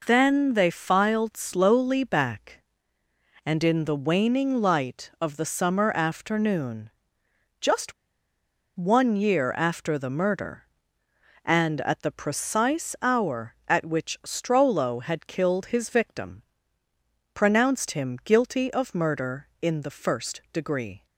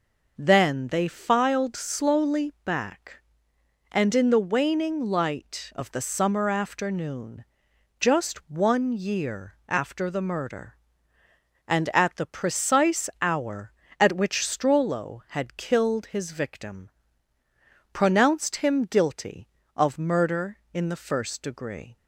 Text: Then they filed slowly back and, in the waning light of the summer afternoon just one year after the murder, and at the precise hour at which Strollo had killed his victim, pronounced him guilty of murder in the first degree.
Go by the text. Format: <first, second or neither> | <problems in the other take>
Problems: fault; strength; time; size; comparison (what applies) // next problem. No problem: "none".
second | pauses between "afternoon" and "just"; noticeable; at 6.8 s; 0.72 s long; noticeable in the second // pauses between "just" and "one"; noticeable; at 7.9 s; 0.83 s long